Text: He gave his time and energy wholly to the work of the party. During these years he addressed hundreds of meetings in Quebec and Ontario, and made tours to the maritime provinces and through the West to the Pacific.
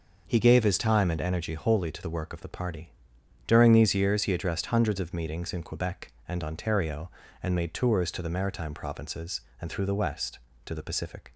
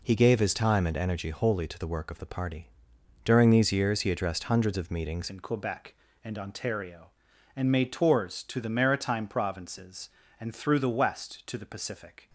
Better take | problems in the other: first | changes voice at "in"; from 5.2 s on; 7.0 s long

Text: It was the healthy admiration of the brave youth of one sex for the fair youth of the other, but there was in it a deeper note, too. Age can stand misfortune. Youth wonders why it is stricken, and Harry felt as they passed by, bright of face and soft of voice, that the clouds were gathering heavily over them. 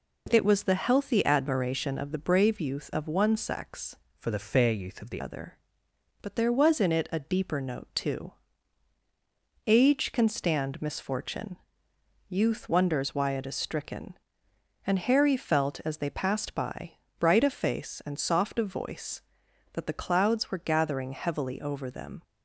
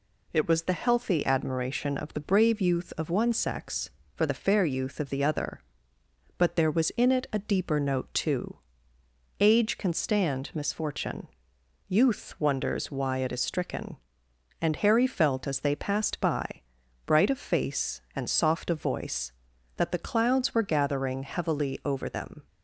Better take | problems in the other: second | changes voice from "for" to "the"; from 4.1 to 5.2 s; 1.1 s long

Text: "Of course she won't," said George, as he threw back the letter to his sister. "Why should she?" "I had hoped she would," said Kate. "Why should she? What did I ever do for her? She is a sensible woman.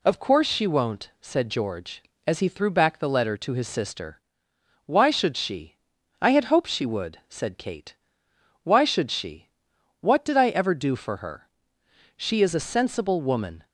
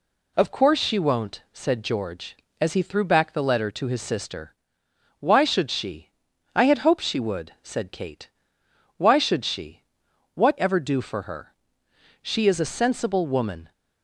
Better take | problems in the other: first | skips "did I"; at 10.5 s

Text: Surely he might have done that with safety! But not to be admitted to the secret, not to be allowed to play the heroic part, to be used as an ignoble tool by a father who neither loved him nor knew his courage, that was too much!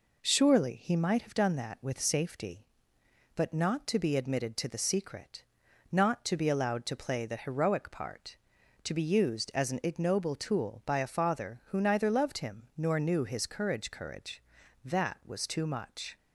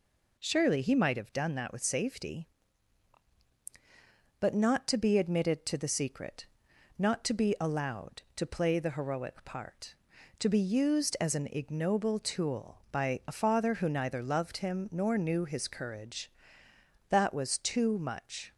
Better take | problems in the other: second | says "courage" twice; at 13.9 s

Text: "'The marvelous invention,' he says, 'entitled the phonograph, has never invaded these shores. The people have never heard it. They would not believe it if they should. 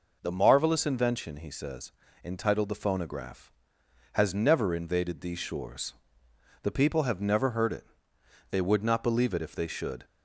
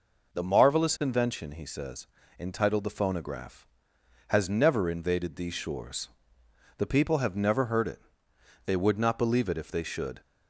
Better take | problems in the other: neither | none

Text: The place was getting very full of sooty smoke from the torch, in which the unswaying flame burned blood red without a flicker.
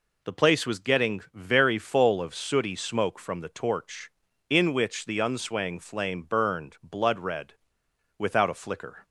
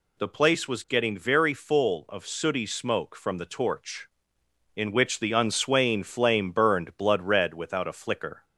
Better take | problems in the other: second | pauses between "red" and "without"; noticeable; at 7.5 s; 0.64 s long

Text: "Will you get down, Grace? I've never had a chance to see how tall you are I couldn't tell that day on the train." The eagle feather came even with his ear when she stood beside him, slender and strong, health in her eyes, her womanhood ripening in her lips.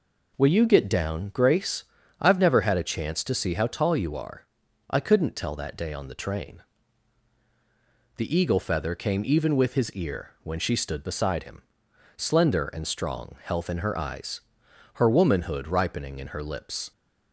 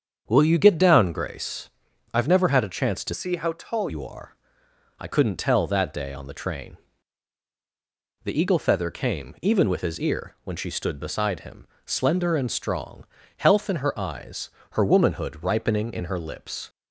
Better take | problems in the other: first | starts louder than the rest; strong; until 1.2 s; 7.5 dB // changes voice from "see" to "tall"; from 3.1 to 3.8 s; 0.7 s long // pauses between "are" and "I"; noticeable; at 4.3 s; 0.64 s long; also in the first

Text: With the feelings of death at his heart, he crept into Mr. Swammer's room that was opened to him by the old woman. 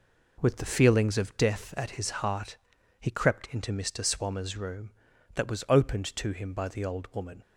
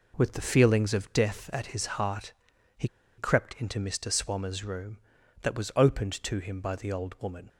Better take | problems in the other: first | pauses between "he" and "crept"; slight; at 2.8 s; 0.31 s long

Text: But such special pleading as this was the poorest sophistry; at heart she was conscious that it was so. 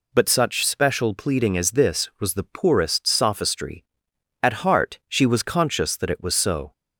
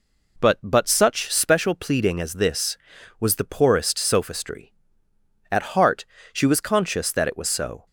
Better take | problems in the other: first | says "But" twice; at 0.6 s // pauses between "heart" and "she"; slight; at 6.0 s; 0.30 s long

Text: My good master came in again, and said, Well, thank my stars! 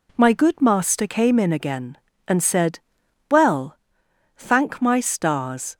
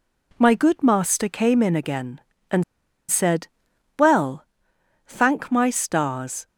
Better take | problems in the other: first | pauses between "and" and "said"; noticeable; at 2.6 s; 0.47 s long

